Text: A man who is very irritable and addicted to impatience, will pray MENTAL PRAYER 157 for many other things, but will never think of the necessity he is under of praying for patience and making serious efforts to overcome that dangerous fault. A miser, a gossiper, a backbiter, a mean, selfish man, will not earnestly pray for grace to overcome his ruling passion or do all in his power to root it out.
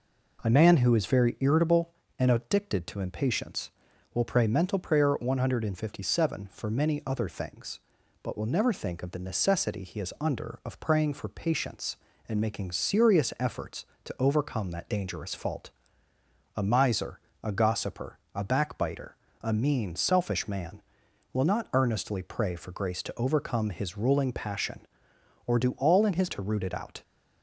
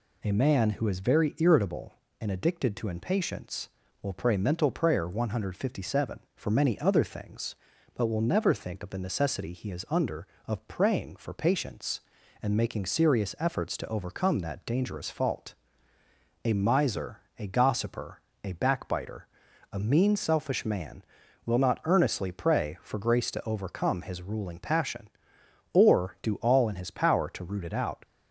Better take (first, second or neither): second